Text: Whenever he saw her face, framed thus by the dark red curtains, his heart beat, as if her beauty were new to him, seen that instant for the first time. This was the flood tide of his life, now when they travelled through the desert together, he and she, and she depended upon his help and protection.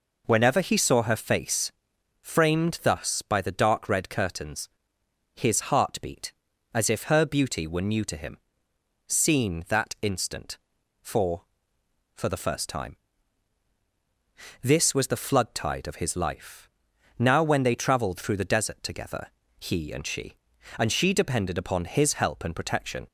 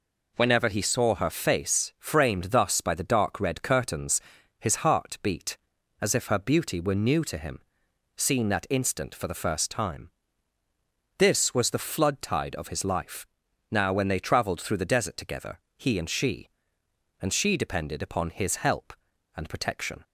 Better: second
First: says "for" twice; at 12.1 s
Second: none

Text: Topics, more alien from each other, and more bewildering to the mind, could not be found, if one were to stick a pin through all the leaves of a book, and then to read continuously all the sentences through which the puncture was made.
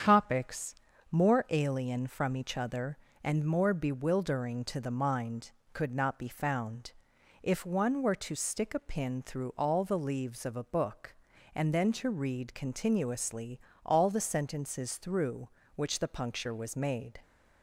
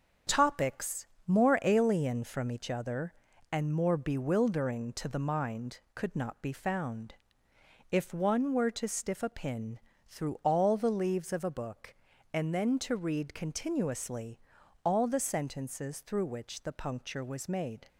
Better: first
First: starts louder than the rest; strong; until 1.4 s; 8 dB // pauses between "continuously" and "all"; slight; at 13.5 s; 0.26 s long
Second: starts louder than the rest; until 1.4 s; 7 dB // says "stiff" for "stick"; at 8.8 s // pauses between "pin" and "through"; slight; at 9.7 s; 0.26 s long // pauses between "continuously" and "all"; noticeable; at 14.3 s; 0.46 s long

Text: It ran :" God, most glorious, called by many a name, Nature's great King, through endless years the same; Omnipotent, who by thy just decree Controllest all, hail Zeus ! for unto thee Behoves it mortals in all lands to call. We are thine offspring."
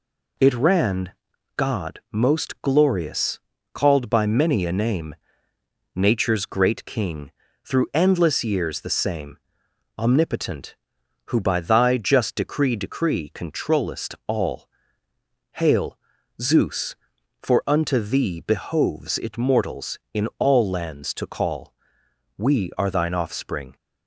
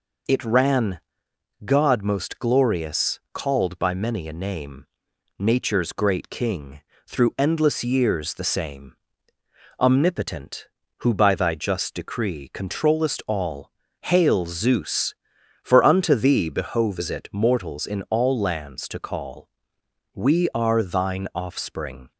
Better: second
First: says "decree" twice; at 12.7 s // pauses between "hail" and "Zeus"; at 15.9 s; 0.42 s long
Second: none

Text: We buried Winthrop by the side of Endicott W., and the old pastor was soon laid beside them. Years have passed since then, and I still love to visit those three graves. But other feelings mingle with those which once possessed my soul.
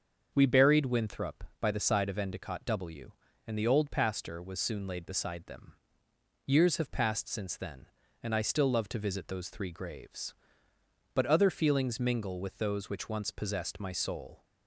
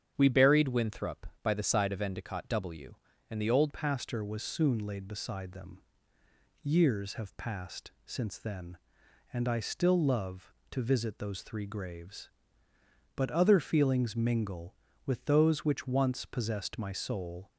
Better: first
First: starts louder than the rest; until 1.3 s; 6.5 dB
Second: starts louder than the rest; strong; until 1.1 s; 8.5 dB // changes voice at "pastor"; from 3.7 s on; 13.8 s long // pauses between "passed" and "since"; slight; at 7.9 s; 0.16 s long

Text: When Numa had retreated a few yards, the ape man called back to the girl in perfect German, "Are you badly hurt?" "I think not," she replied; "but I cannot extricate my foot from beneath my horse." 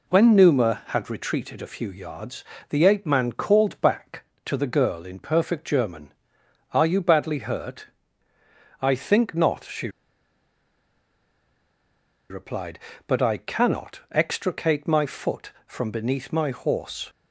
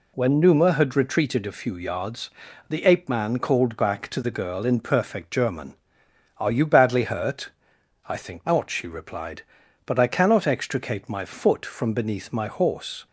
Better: second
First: pauses between "she" and "replied"; strong; at 9.8 s; 2.4 s long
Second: none

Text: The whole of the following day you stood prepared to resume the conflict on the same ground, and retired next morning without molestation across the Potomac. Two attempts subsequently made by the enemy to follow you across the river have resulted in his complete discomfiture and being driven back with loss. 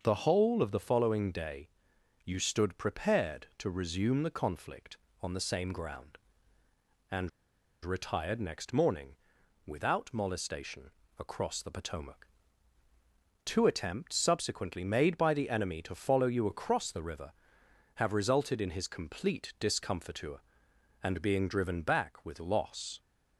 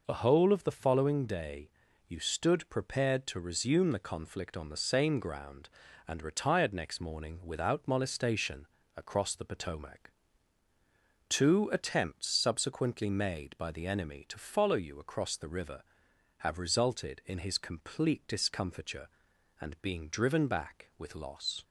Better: second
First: starts louder than the rest; until 1.0 s; 6.5 dB // pauses between "day" and "you"; noticeable; at 1.7 s; 0.54 s long // pauses between "and" and "retired"; noticeable; at 7.2 s; 0.55 s long // pauses between "morning" and "without"; noticeable; at 9.1 s; 0.50 s long // pauses between "molestation" and "across"; slight; at 10.9 s; 0.26 s long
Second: pauses between "day" and "you"; at 1.7 s; 0.38 s long // pauses between "molestation" and "across"; slight; at 8.6 s; 0.28 s long

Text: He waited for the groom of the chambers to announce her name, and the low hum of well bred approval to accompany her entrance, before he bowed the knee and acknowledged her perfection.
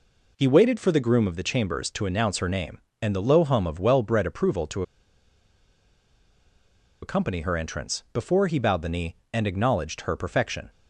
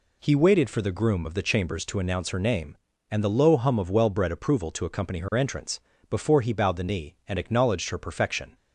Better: second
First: pauses between "to" and "accompany"; strong; at 4.8 s; 2.1 s long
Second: none

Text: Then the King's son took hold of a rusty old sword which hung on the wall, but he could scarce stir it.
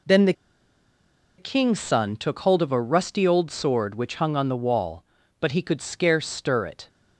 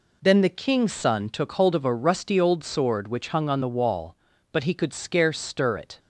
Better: second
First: pauses between "the" and "King's"; at 0.3 s; 1.0 s long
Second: none

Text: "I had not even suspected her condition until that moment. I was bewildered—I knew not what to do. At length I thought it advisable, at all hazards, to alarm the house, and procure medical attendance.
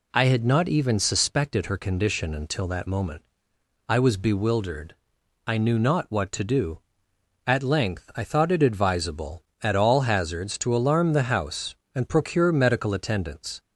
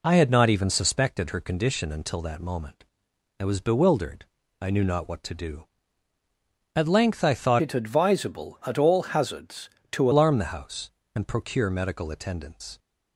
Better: first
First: none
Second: changes voice from "it" to "to"; from 7.6 to 10.1 s; 2.5 s long

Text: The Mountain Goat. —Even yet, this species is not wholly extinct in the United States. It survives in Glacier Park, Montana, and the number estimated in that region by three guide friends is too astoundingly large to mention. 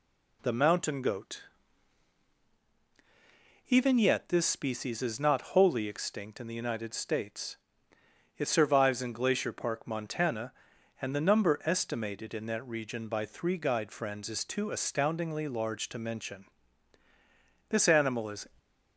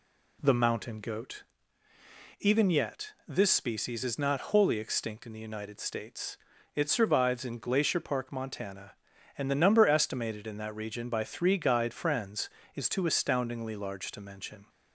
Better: second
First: goes on to say "This animal is"; noticeable; from 17.6 s on; 0.78 s long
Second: none

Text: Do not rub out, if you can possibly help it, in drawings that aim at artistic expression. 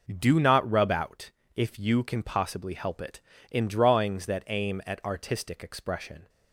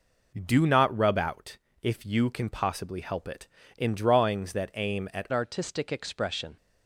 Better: first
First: none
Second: changes voice at "artistic"; from 5.3 s on; 1.2 s long

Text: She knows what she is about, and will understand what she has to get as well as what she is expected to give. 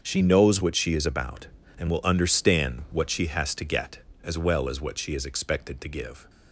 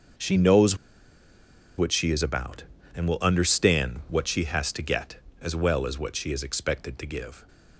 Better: first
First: starts louder than the rest; until 1.0 s; 7 dB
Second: starts louder than the rest; until 2.2 s; 7 dB // pauses between "knows" and "what"; at 0.7 s; 1.0 s long

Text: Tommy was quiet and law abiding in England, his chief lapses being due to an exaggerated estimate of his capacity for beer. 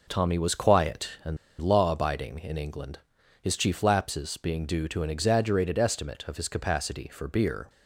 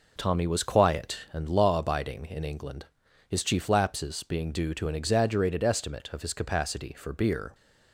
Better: second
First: pauses between "and" and "law"; slight; at 1.3 s; 0.23 s long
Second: none

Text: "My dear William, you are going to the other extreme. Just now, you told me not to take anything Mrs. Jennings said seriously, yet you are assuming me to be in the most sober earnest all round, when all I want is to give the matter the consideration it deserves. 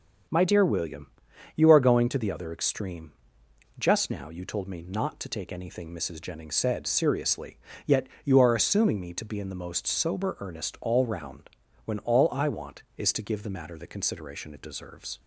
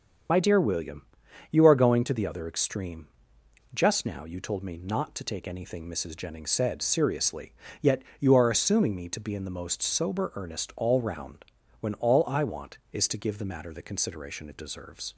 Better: first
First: pauses between "yet" and "you"; slight; at 8.0 s; 0.16 s long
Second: loses the start of "My"; at 0.2 s; 50 ms // starts louder than the rest; until 1.7 s; 7 dB // pauses between "yet" and "you"; slight; at 8.0 s; 0.16 s long

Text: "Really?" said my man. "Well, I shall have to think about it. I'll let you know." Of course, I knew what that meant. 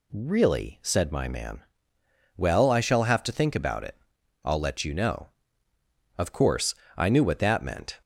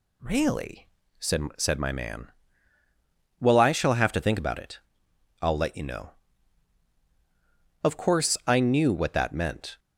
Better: first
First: none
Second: says "said" twice; at 1.5 s

